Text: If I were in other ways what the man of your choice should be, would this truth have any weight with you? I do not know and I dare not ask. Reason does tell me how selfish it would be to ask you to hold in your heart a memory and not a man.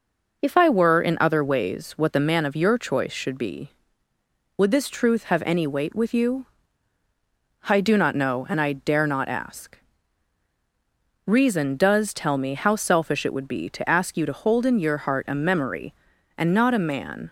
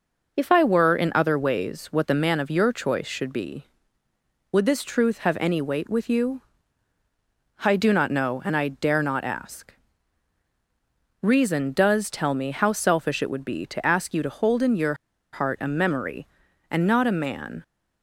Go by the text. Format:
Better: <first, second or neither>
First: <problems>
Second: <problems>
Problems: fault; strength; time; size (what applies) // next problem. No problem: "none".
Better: first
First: none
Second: pauses between "your" and "heart"; at 14.9 s; 0.38 s long